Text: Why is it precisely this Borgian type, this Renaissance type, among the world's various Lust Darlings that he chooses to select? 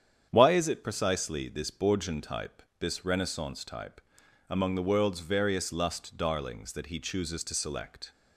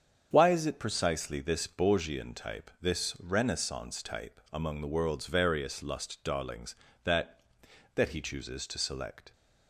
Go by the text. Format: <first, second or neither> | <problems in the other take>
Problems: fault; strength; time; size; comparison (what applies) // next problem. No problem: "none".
first | starts louder than the rest; strong; until 1.3 s; 7.5 dB; strong in the first // says "that" twice; at 7.9 s